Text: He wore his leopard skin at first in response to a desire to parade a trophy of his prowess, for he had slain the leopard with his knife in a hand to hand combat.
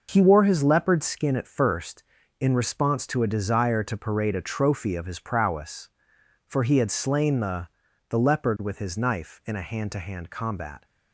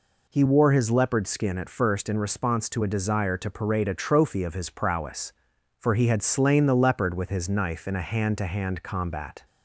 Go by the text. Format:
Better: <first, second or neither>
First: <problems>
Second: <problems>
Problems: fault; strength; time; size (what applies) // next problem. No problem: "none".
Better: second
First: says "the" twice; at 8.0 s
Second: none